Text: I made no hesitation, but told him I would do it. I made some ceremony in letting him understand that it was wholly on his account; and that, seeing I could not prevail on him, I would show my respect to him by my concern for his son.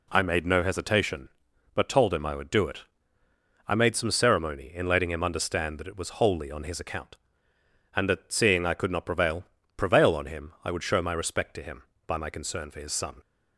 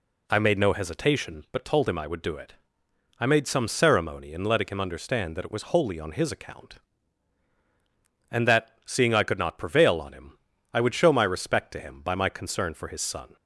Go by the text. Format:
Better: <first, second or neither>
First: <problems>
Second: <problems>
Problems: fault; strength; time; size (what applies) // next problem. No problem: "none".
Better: second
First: says "prevail" twice; at 9.7 s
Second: none